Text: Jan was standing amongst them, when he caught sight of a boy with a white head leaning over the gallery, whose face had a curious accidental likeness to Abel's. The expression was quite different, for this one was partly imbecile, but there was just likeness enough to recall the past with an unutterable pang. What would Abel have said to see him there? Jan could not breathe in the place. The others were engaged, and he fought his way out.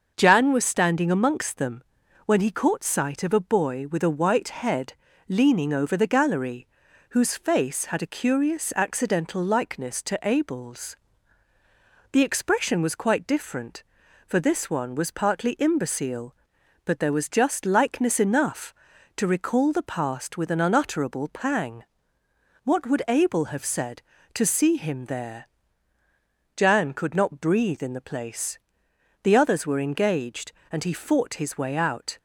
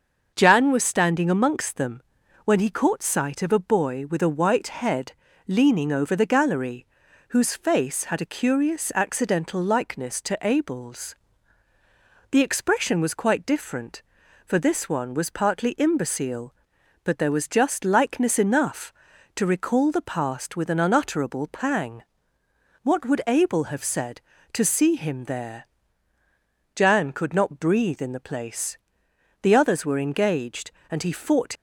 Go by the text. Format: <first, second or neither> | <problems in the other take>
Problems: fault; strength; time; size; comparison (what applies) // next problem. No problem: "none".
first | starts louder than the rest; until 1.3 s; 6.5 dB; also in the first // pauses between "head" and "leaning"; slight; at 5.1 s; 0.34 s long; slight in the first // stops before "his way out"; at 31.5 s